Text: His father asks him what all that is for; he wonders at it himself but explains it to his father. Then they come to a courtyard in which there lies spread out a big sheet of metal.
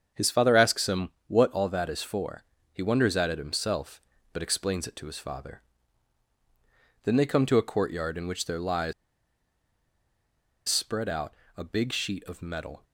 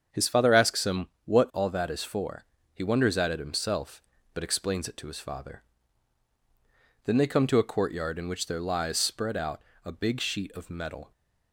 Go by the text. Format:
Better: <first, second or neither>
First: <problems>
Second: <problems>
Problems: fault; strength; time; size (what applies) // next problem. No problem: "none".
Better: second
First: starts louder than the rest; strong; until 1.3 s; 7.5 dB // pauses between "him" and "what"; slight; at 1.1 s; 0.16 s long // pauses between "lies" and "spread"; strong; at 8.9 s; 1.7 s long // pauses between "out" and "a"; slight; at 11.3 s; 0.22 s long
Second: starts louder than the rest; strong; until 1.2 s; 7 dB // pauses between "him" and "what"; slight; at 1.0 s; 0.16 s long // pauses between "out" and "a"; slight; at 9.6 s; 0.22 s long